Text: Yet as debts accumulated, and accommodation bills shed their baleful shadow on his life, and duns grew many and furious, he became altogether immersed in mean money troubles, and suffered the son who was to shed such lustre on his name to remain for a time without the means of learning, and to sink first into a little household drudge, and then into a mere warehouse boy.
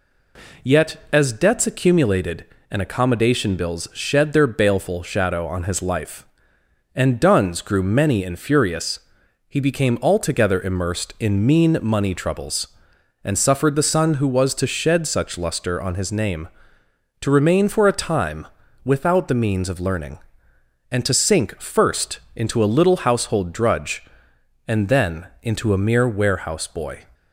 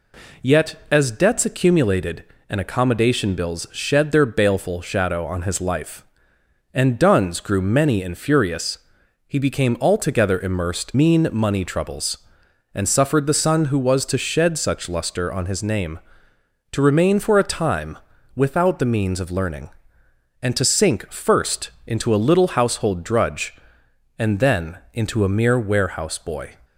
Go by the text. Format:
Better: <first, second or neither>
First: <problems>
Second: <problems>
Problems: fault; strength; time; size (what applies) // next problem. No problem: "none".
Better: first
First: pauses between "time" and "without"; at 18.4 s; 0.38 s long // pauses between "first" and "into"; slight; at 22.1 s; 0.16 s long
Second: skips "in"; at 10.9 s // pauses between "time" and "without"; at 17.9 s; 0.38 s long // pauses between "first" and "into"; slight; at 21.7 s; 0.16 s long